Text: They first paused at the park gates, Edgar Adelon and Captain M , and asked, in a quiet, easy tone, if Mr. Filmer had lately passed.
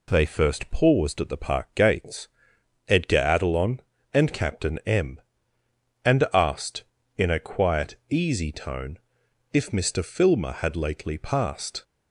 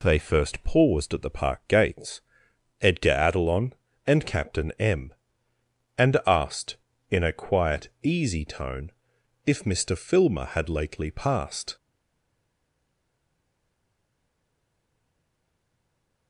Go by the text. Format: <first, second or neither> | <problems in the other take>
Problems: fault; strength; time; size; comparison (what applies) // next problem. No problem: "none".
first | stays silent after the last word; strong; from 11.7 s on; 4.5 s long